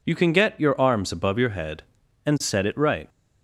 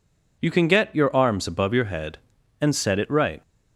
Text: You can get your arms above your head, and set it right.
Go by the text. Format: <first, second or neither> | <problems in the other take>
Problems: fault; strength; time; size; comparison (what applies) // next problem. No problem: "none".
neither | none